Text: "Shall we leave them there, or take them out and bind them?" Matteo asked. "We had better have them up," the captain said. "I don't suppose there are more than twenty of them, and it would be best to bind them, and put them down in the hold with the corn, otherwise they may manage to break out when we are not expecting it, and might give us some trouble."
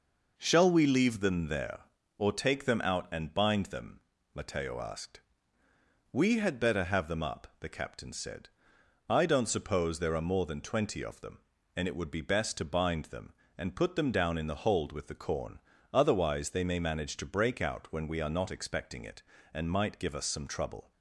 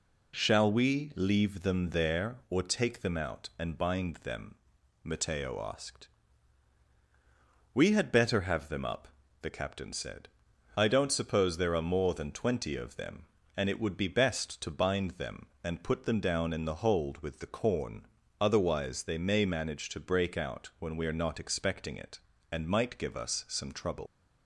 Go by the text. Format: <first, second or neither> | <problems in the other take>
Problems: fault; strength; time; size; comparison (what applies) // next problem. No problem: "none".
first | leaves "trouble" unfinished; at 24.0 s; 70 ms